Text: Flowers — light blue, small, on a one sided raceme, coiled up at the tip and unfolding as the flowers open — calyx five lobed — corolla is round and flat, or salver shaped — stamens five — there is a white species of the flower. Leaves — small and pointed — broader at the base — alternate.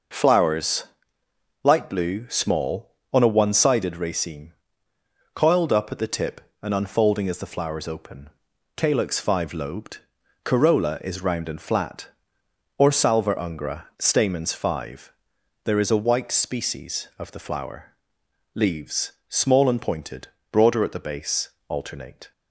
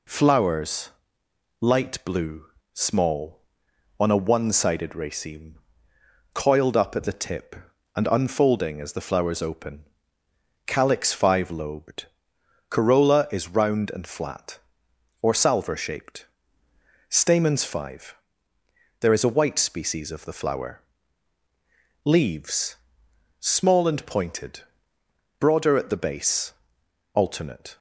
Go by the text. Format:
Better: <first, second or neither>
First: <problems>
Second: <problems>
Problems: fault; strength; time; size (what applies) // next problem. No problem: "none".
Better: second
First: says "ungra" for "shaped"; at 13.3 s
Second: none